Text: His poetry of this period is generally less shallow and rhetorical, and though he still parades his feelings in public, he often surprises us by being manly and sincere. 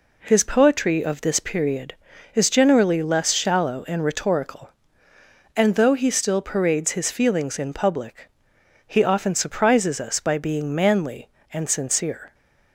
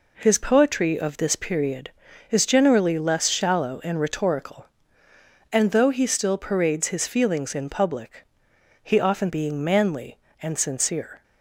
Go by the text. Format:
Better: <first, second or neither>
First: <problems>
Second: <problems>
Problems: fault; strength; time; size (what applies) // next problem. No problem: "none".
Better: first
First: none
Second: skips "surprises us by"; at 9.2 s